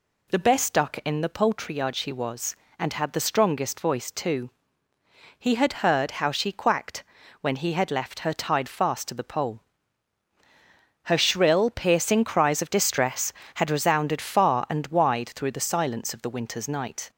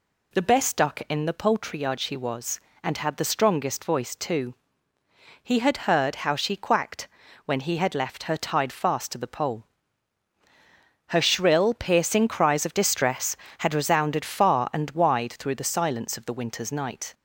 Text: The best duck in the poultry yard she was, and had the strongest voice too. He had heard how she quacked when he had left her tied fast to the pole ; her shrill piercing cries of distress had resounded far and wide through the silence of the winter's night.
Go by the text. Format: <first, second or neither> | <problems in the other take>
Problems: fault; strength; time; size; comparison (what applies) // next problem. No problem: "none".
neither | pauses between "quacked" and "when"; the same in both